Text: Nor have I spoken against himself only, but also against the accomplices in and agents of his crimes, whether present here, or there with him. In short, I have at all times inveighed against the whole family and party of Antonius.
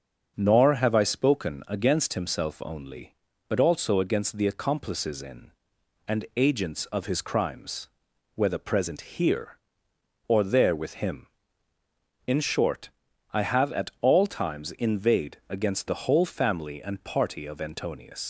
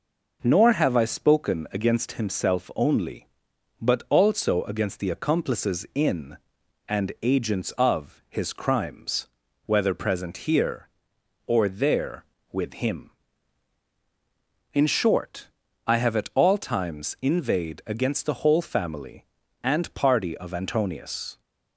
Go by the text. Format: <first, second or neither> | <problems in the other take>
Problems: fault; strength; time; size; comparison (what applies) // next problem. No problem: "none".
second | starts louder than the rest; until 1.3 s; 6.5 dB // leaves "Antonius" unfinished; at 18.2 s; 80 ms